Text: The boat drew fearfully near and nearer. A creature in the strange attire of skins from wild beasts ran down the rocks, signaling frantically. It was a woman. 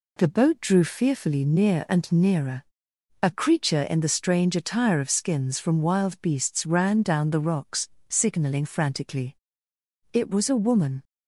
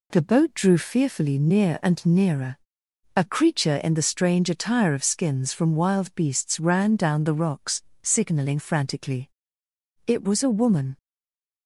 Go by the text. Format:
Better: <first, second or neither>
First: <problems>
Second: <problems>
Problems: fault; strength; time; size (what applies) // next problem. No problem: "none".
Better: first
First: none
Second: stays silent after the last word; slight; from 10.9 s on; 0.7 s long